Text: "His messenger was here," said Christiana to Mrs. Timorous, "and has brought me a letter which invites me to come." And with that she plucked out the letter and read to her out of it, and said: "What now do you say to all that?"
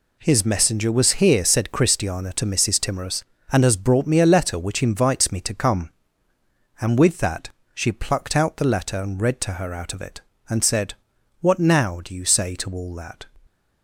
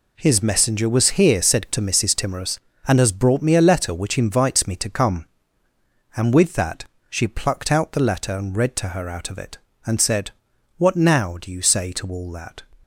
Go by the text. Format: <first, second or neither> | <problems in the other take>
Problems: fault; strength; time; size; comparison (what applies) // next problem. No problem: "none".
first | skips "Christiana"; at 1.6 s // pauses between "that" and "she"; slight; at 6.8 s; 0.24 s long; slight in the first